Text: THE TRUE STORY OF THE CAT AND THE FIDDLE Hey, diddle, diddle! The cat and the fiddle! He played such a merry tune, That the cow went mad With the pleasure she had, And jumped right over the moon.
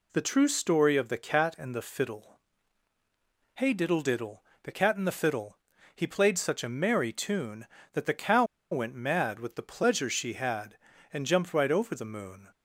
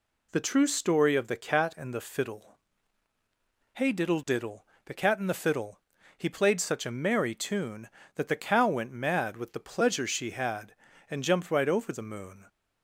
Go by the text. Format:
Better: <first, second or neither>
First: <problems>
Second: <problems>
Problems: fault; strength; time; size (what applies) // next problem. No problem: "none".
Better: second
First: pauses between "FIDDLE" and "Hey"; at 2.3 s; 1.1 s long // pauses between "cow" and "went"; slight; at 8.4 s; 0.27 s long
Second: pauses between "FIDDLE" and "Hey"; at 2.5 s; 1.1 s long